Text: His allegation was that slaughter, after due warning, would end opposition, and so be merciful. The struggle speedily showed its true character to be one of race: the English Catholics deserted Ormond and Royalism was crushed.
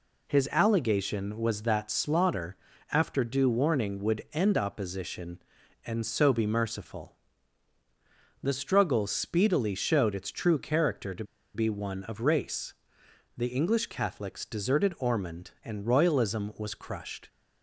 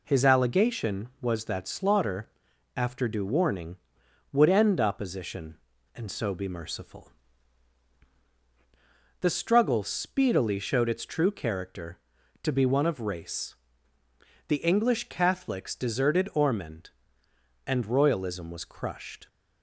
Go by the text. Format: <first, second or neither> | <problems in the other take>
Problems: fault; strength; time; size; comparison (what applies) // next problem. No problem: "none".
second | pauses between "to" and "be"; slight; at 11.2 s; 0.31 s long